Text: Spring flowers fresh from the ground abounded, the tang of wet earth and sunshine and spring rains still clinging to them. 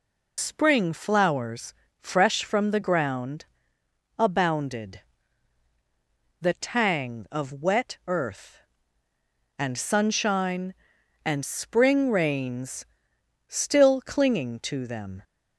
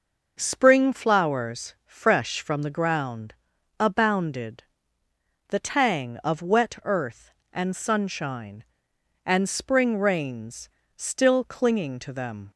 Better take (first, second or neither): second